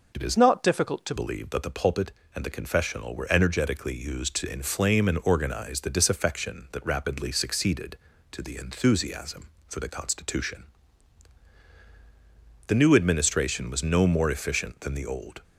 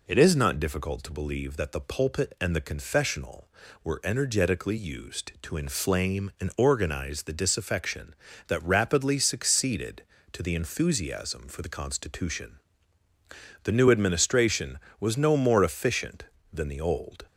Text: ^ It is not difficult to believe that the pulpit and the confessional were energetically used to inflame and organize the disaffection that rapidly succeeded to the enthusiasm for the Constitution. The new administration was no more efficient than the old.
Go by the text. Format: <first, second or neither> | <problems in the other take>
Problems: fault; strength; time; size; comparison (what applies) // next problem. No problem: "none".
second | changes voice from "not" to "to"; from 0.3 to 1.1 s; 0.8 s long